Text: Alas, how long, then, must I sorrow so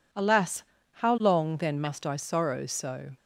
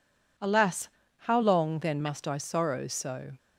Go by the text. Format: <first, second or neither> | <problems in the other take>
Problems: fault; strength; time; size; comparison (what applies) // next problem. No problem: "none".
neither | none